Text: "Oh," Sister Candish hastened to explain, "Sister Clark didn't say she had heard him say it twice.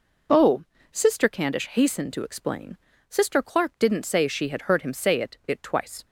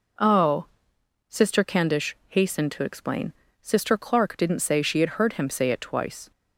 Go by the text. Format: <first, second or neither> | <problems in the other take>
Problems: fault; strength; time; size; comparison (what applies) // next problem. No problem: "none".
second | says "it" twice; at 5.4 s